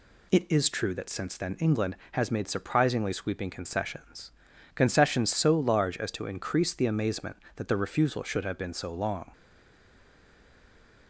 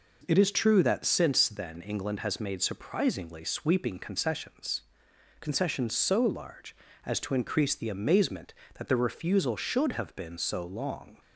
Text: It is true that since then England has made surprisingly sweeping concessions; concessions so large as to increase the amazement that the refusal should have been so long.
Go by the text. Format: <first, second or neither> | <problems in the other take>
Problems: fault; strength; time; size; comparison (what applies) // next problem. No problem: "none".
second | stays silent after the last word; noticeable; from 9.3 s on; 1.7 s long